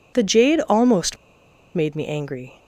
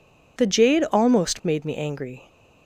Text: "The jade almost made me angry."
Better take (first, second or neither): second